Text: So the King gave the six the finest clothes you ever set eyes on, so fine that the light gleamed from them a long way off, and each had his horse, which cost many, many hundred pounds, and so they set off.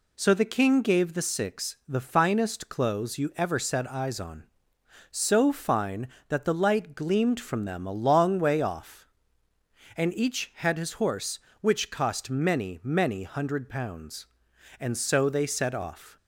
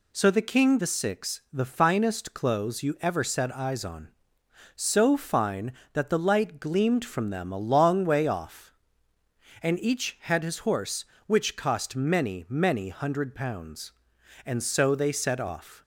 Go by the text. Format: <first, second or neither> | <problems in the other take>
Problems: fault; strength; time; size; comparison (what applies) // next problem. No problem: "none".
first | skips "gave"; at 0.7 s